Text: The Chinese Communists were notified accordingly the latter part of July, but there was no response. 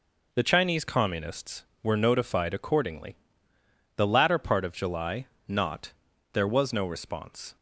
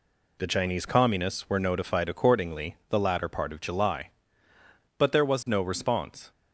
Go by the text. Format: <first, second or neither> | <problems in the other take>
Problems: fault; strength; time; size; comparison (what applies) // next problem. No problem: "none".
second | pauses between "accordingly" and "the"; noticeable; at 3.1 s; 0.80 s long // says "not" for "but"; at 5.4 s